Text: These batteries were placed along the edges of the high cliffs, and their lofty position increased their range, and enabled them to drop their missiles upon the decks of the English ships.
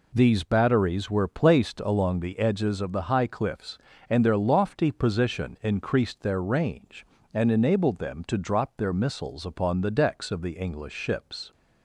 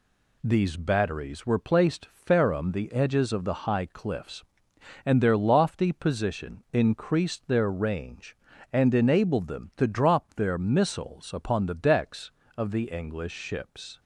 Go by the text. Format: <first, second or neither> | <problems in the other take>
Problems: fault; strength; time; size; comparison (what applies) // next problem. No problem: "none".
first | says "ferrum" for "along"; at 2.0 s